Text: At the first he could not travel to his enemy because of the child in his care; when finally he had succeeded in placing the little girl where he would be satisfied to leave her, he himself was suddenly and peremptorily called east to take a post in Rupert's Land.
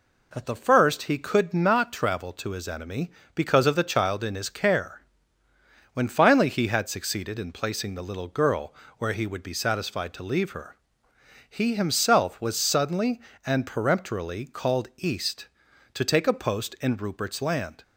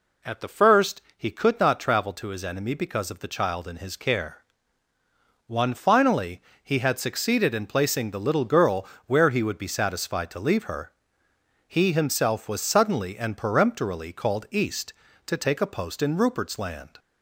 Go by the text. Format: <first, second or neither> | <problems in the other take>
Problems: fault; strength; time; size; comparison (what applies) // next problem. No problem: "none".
first | pauses between "first" and "he"; slight; at 1.0 s; 0.16 s long // says "one" for "when"; at 5.4 s // pauses between "finally" and "he"; slight; at 6.4 s; 0.18 s long // pauses between "girl" and "where"; slight; at 8.8 s; 0.22 s long; slight in the first